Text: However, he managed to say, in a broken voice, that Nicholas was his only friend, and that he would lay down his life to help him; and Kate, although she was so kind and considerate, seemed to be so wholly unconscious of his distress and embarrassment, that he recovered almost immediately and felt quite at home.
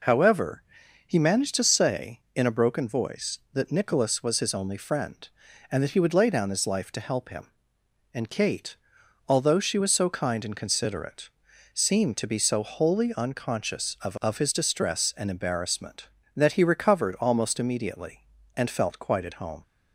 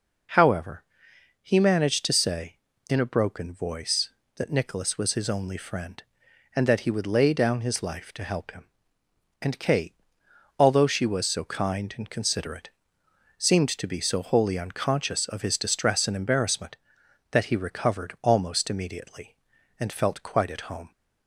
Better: second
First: says "of" twice; at 14.1 s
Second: none

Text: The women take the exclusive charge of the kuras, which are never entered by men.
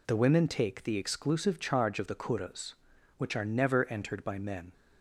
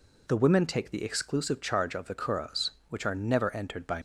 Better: first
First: none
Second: stops before "men"; at 3.9 s

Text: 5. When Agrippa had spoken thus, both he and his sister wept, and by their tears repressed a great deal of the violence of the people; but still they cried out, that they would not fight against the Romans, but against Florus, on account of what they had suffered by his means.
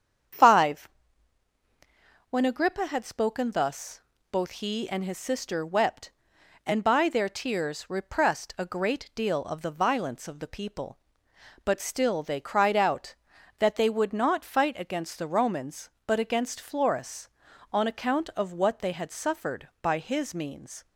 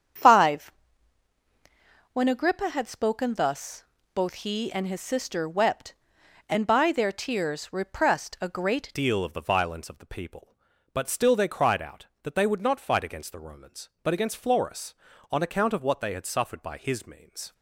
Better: first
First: starts louder than the rest; strong; until 2.7 s; 8 dB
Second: starts louder than the rest; strong; until 2.6 s; 8 dB // changes voice at "deal"; from 8.9 s on; 8.6 s long

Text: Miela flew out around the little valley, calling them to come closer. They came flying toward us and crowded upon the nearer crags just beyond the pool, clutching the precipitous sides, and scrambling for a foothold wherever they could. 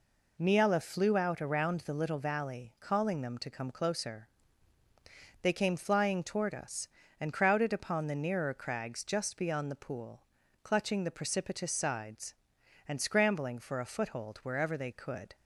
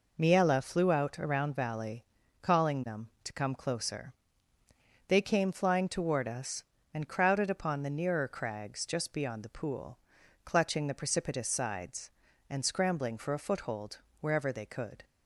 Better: first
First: none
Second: skips "the little"; at 1.5 s // pauses between "foothold" and "wherever"; slight; at 13.9 s; 0.22 s long

